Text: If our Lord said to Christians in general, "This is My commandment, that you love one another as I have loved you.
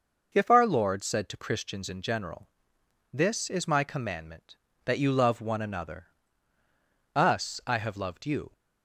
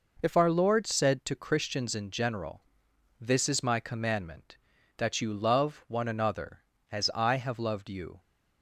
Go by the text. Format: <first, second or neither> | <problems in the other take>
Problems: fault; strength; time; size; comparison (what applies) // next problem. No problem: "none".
second | says "us" for "as"; at 7.1 s